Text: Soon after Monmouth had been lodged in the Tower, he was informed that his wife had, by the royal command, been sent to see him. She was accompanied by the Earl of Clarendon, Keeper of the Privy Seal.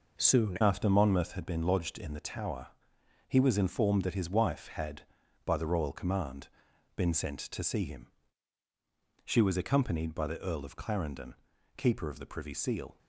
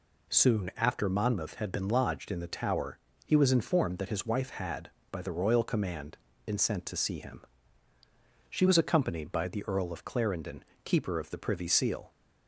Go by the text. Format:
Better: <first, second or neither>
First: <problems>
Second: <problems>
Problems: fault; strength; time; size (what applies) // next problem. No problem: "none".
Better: second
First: changes voice at "after"; from 0.6 s on; 12.3 s long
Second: none